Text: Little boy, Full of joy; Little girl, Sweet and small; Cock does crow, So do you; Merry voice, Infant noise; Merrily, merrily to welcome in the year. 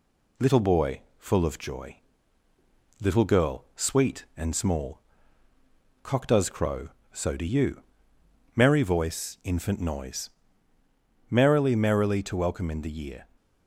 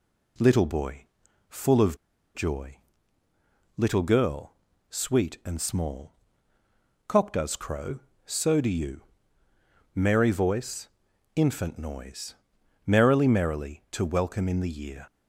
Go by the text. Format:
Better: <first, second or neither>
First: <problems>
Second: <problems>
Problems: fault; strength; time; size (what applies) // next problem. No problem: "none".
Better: first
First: none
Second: pauses between "of" and "joy"; at 1.9 s; 0.37 s long